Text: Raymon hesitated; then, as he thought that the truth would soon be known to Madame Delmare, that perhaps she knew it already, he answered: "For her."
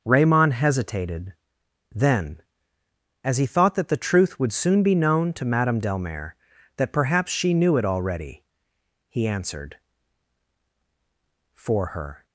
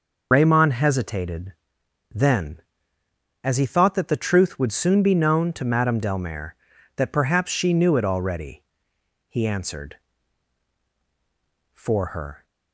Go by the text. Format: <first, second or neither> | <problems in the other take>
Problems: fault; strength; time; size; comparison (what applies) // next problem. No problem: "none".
first | loses the start of "Raymon"; at 0.3 s; 85 ms